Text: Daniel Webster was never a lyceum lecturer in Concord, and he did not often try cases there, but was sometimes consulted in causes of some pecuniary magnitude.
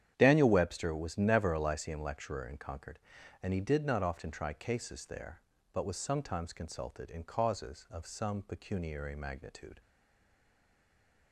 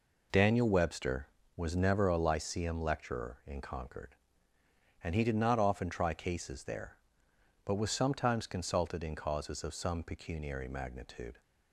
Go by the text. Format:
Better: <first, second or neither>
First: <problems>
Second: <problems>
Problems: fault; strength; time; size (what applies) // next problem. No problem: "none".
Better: second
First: starts louder than the rest; strong; until 1.1 s; 9.5 dB // stays silent after the last word; noticeable; from 9.8 s on; 1.5 s long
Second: none